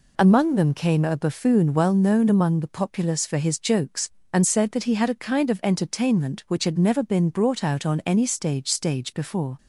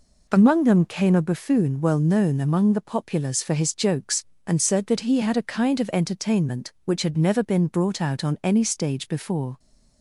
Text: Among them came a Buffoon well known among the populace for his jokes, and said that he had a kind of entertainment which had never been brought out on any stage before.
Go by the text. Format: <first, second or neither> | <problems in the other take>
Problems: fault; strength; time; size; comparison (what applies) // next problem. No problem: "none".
second | says "stage" twice; at 8.7 s